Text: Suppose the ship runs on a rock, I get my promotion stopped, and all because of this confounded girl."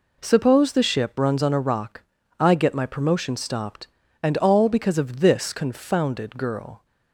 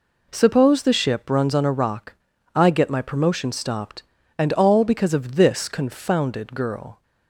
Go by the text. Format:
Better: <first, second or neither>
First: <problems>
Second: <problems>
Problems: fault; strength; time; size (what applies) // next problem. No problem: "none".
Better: neither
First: none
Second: none